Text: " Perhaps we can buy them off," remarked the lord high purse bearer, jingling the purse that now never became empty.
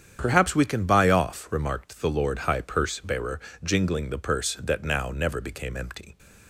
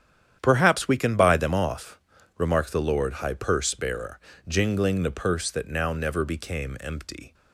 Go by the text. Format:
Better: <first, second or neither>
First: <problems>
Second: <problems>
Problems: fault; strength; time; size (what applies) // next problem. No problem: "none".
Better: second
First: starts louder than the rest; strong; until 1.2 s; 8.5 dB // skips "them"; at 1.0 s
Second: starts louder than the rest; strong; until 1.4 s; 9.5 dB